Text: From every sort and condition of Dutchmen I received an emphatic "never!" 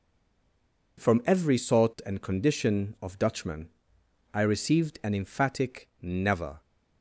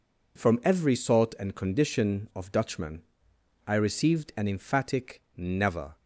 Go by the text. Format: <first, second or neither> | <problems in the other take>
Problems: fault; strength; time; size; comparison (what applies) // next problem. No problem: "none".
second | stays silent before the first word; slight; until 0.9 s; 0.9 s long // pauses between "Dutchmen" and "I"; noticeable; at 3.6 s; 0.66 s long; noticeable in the second